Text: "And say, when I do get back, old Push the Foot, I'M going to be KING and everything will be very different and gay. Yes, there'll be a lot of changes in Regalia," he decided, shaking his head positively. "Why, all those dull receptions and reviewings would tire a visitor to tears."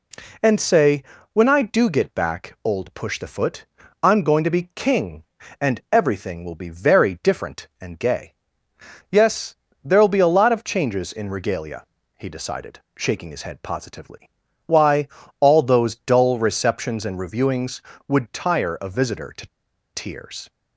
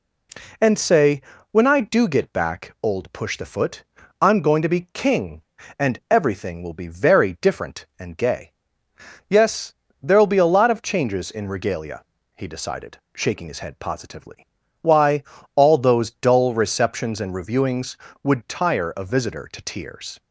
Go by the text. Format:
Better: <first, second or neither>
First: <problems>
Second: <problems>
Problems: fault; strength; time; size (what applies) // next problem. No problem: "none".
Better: second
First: pauses between "to" and "tears"; noticeable; at 19.4 s; 0.47 s long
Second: none